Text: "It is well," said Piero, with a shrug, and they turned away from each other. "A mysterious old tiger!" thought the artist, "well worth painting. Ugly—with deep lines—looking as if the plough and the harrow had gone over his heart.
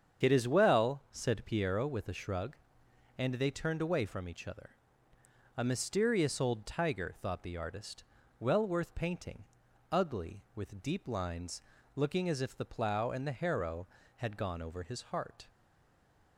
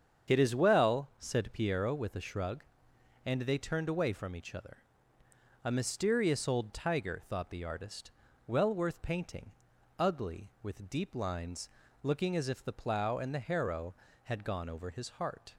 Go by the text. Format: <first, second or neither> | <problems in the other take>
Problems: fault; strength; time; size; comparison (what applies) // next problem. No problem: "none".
second | starts louder than the rest; strong; until 1.3 s; 7.5 dB; strong in the second // stays silent after the last word; slight; from 15.4 s on; 0.9 s long